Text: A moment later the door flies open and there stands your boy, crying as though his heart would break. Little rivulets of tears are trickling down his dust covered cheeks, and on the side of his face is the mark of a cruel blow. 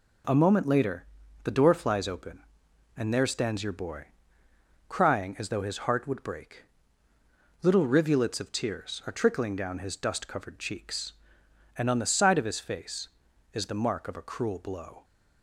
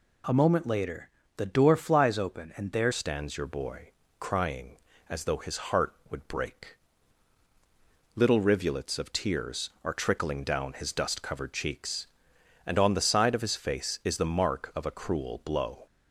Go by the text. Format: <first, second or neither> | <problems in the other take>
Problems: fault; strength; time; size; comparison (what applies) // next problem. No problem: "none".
first | pauses between "later" and "the"; slight; at 1.0 s; 0.28 s long; also in the first // changes voice at "stands"; from 2.9 s on; 12.9 s long